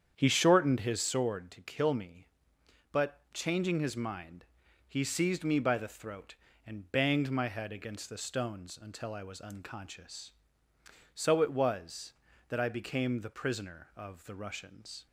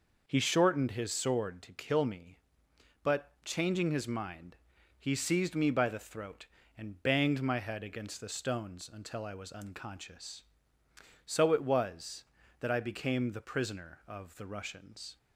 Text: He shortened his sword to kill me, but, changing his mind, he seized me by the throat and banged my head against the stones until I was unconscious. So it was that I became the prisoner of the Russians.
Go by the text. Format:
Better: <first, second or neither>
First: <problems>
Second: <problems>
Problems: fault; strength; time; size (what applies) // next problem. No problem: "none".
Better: second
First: starts louder than the rest; strong; until 1.2 s; 8.5 dB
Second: none